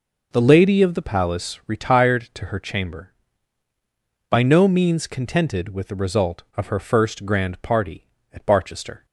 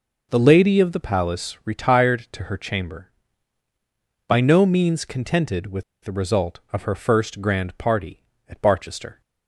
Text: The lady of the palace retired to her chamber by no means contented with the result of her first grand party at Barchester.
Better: first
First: none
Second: pauses between "with" and "the"; slight; at 5.8 s; 0.21 s long

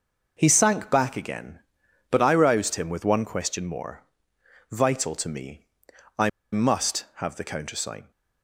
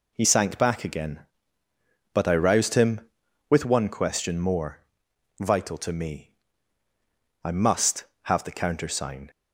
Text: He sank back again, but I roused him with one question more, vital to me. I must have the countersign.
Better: second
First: pauses between "I" and "must"; slight; at 6.2 s; 0.22 s long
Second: none

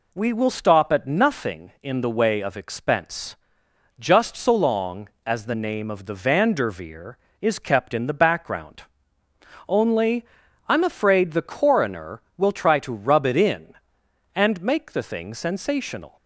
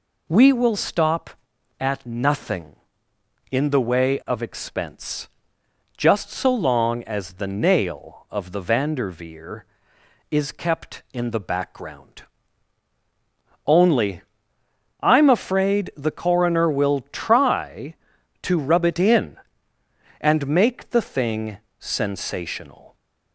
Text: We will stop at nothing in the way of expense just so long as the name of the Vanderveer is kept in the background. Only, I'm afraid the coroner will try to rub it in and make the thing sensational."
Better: first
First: pauses between "expense" and "just"; noticeable; at 3.3 s; 0.62 s long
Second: pauses between "expense" and "just"; noticeable; at 5.2 s; 0.68 s long // says "nail" for "name"; at 7.4 s // pauses between "thing" and "sensational"; slight; at 21.5 s; 0.22 s long

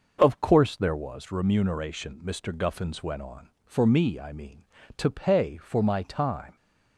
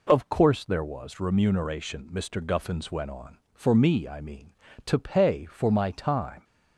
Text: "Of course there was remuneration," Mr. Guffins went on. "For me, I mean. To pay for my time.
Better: second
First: starts louder than the rest; noticeable; until 1.3 s; 6 dB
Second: none

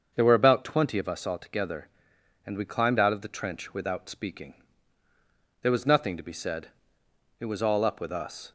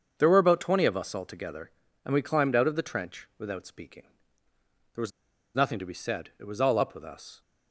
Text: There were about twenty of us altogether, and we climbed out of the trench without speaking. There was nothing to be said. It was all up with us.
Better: first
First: starts louder than the rest; until 1.1 s; 6.5 dB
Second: starts louder than the rest; until 1.1 s; 7 dB // pauses between "was" and "nothing"; at 5.1 s; 0.43 s long

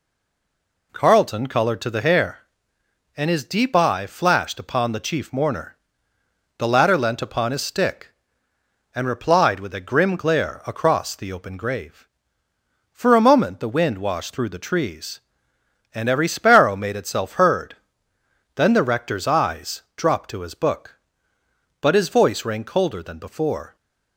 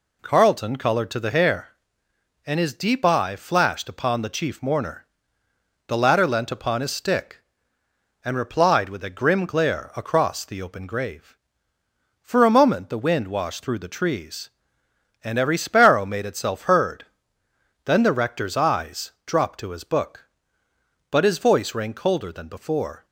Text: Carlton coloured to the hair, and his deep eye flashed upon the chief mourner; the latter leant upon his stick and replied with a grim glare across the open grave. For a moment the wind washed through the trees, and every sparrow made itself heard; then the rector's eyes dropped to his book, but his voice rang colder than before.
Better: second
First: stays silent before the first word; slight; until 0.9 s; 0.9 s long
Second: none

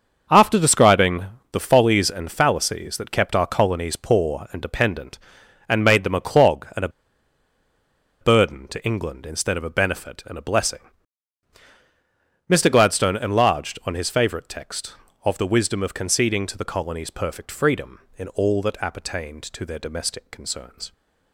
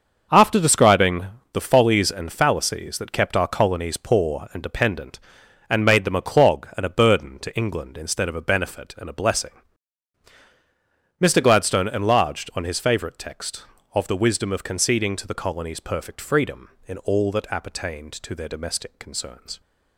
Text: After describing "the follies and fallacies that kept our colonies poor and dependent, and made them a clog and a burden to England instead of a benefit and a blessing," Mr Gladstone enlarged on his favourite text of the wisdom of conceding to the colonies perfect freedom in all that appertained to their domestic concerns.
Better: second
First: starts louder than the rest; until 1.5 s; 6.5 dB // pauses between "describing" and "the"; slight; at 1.2 s; 0.28 s long // pauses between "a" and "burden"; strong; at 6.8 s; 1.3 s long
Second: starts louder than the rest; until 1.6 s; 6.5 dB // pauses between "describing" and "the"; slight; at 1.2 s; 0.28 s long

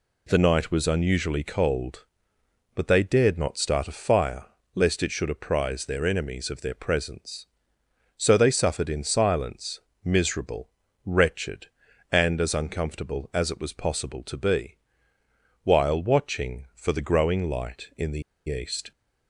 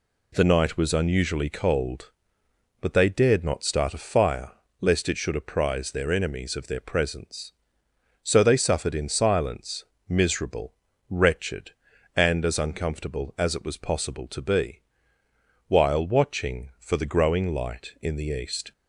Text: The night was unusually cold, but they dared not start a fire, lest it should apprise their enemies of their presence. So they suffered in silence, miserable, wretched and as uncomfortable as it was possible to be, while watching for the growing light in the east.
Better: second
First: pauses between "the" and "east"; slight; at 18.2 s; 0.26 s long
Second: none

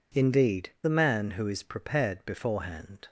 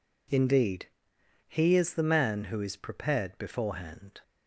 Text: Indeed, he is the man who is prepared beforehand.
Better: second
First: skips "he is"; at 0.7 s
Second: none

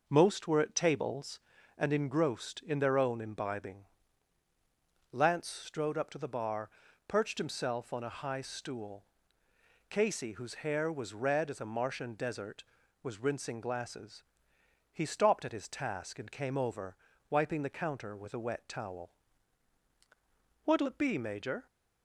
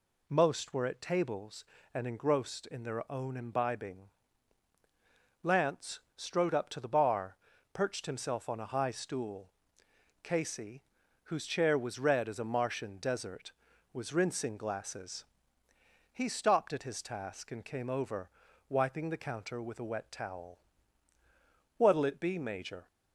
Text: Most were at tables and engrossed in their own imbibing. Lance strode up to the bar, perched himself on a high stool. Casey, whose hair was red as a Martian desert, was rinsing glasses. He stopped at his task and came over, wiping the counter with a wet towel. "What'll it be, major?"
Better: first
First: none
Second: pauses between "Lance" and "strode"; slight; at 5.9 s; 0.18 s long // says "chair" for "hair"; at 11.4 s

